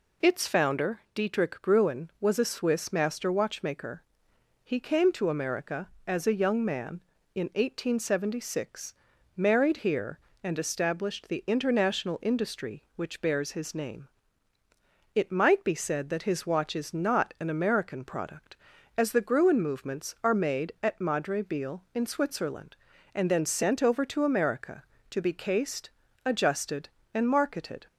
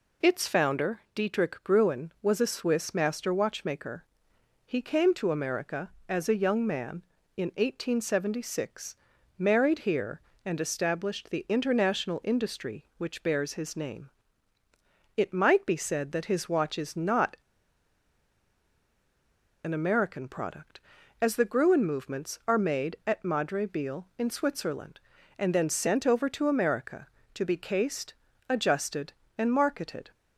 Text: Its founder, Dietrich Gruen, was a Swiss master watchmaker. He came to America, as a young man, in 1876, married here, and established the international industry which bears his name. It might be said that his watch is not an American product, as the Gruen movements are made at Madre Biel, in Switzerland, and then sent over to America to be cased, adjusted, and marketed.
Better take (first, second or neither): first